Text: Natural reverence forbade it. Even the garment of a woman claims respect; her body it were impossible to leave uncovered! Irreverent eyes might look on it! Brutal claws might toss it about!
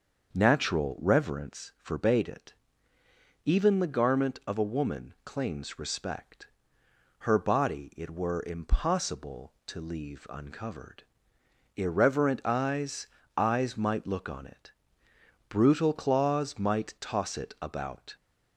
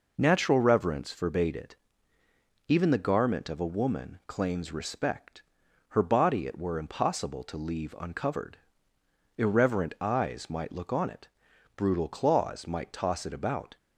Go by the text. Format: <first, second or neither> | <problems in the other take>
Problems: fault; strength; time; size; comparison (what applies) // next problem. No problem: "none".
second | starts louder than the rest; until 1.3 s; 6.5 dB // says "eyes" twice; at 13.3 s